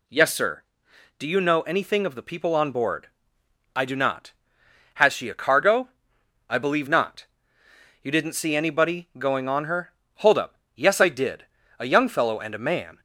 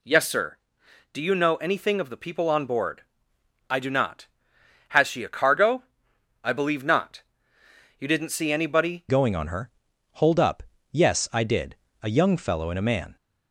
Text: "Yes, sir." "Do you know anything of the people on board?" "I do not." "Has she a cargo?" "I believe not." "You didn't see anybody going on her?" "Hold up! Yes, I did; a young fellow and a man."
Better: first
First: none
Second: changes voice at "going"; from 9.0 s on; 4.1 s long

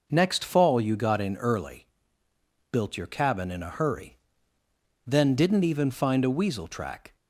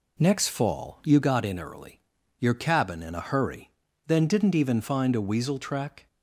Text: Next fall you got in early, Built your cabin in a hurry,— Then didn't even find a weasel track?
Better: first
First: none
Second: skips "Built"; at 2.1 s

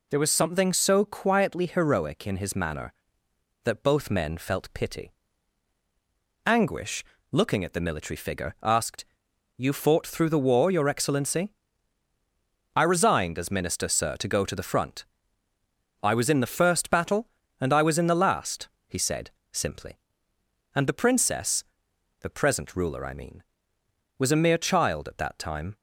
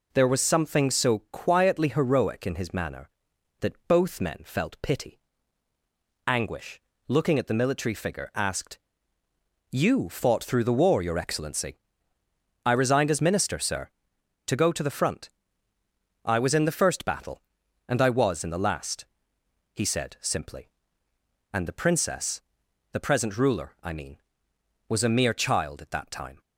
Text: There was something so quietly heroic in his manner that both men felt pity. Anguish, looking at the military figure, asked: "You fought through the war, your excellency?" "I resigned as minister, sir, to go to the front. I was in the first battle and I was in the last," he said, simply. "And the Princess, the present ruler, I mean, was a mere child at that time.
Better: neither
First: none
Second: none

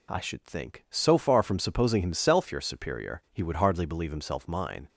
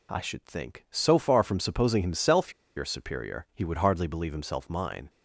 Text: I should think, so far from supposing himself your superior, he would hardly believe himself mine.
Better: first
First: none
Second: pauses between "himself" and "your"; slight; at 2.5 s; 0.24 s long

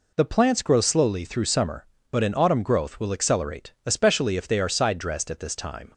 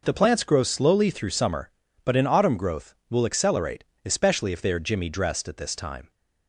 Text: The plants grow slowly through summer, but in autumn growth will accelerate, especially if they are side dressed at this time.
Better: first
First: none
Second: says "jimmy" for "side"; at 4.8 s

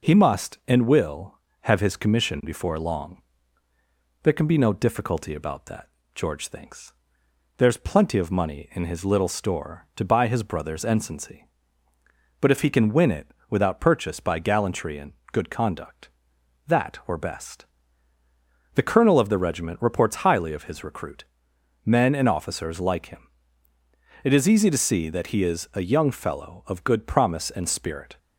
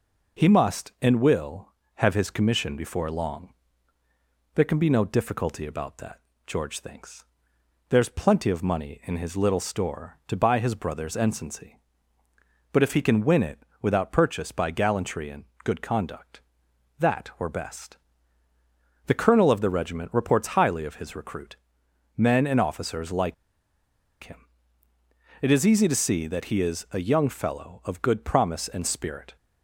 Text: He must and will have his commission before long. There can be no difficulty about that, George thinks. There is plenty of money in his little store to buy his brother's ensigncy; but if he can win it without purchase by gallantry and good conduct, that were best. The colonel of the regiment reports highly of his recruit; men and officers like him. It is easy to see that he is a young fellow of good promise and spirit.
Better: first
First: pauses between "it" and "without"; slight; at 13.3 s; 0.18 s long // pauses between "and" and "good"; slight; at 15.1 s; 0.18 s long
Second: pauses between "it" and "without"; slight; at 13.6 s; 0.18 s long // pauses between "and" and "good"; slight; at 15.4 s; 0.18 s long // pauses between "like" and "him"; noticeable; at 23.3 s; 0.88 s long

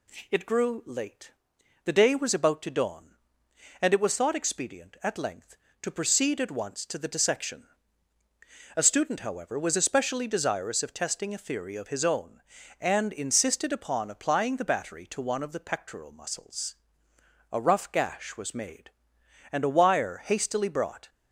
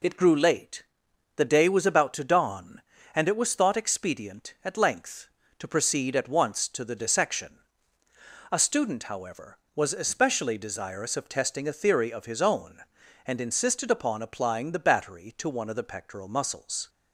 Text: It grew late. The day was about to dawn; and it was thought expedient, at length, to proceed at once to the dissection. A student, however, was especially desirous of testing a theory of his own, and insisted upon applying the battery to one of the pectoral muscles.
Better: second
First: goes on to say "A rough gash was made and a wire hastily brought"; strong; from 17.5 s on; 3.5 s long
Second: none

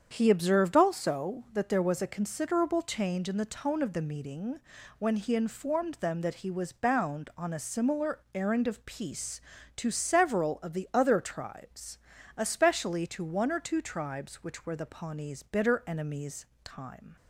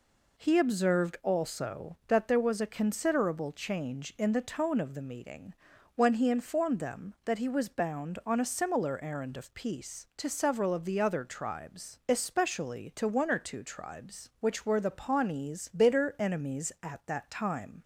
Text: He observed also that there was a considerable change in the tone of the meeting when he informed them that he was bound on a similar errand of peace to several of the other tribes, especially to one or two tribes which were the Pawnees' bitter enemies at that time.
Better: second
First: starts louder than the rest; strong; until 1.1 s; 7.5 dB // pauses between "meeting" and "when"; at 4.5 s; 0.38 s long // skips "at that"; at 16.5 s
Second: pauses between "meeting" and "when"; at 5.5 s; 0.40 s long

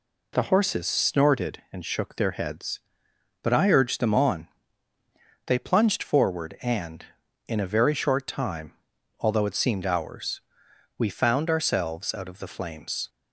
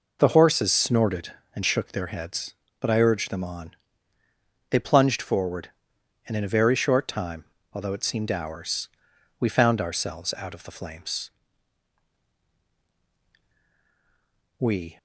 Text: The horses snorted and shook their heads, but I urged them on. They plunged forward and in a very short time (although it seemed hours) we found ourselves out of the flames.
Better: first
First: none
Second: goes on to say "We"; slight; from 14.5 s on; 0.40 s long

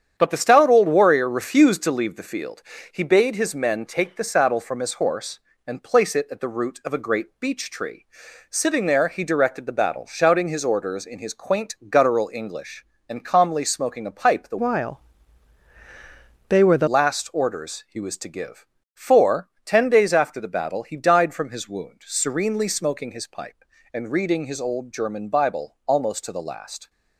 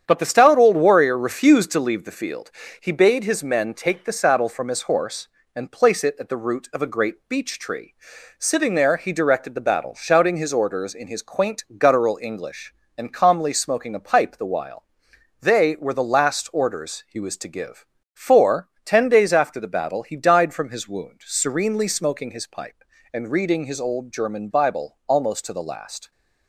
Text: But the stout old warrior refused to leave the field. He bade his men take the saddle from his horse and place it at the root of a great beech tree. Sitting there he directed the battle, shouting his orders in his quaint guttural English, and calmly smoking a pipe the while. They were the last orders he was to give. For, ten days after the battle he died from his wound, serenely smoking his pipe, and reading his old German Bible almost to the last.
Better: second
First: starts louder than the rest; strong; until 1.1 s; 8.5 dB // changes voice from "while" to "the"; from 14.5 to 16.8 s; 2.3 s long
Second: starts louder than the rest; strong; until 1.0 s; 8.5 dB

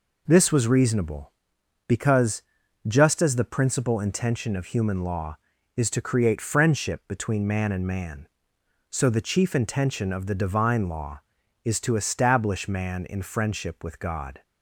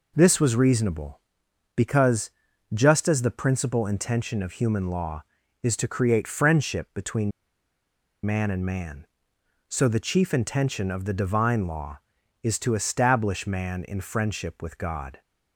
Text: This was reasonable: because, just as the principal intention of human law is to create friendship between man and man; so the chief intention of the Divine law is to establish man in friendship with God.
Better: first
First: none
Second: pauses between "between" and "man"; noticeable; at 7.3 s; 0.93 s long

